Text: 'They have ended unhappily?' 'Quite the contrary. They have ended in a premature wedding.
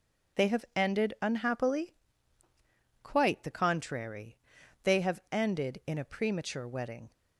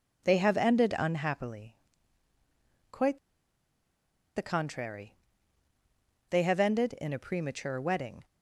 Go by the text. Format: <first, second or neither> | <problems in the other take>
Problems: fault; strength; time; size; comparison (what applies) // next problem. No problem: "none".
first | pauses between "Quite" and "the"; at 3.1 s; 1.1 s long